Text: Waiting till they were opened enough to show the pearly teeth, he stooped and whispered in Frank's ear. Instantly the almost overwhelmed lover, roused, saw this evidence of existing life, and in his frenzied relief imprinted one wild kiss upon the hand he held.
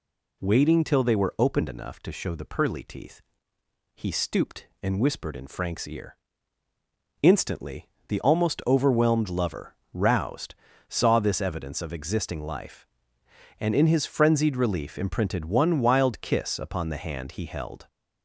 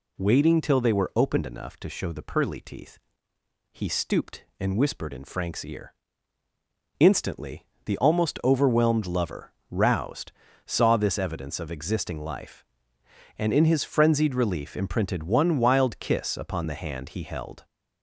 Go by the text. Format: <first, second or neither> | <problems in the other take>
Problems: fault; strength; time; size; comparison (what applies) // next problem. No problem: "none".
neither | pauses between "Instantly" and "the"; slight; the same in both